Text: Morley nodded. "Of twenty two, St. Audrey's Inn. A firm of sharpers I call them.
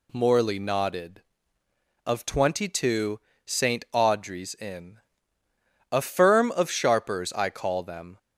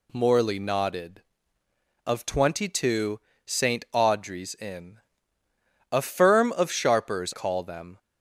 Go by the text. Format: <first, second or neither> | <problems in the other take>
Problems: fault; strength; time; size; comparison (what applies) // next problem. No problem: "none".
first | skips "I"; at 7.3 s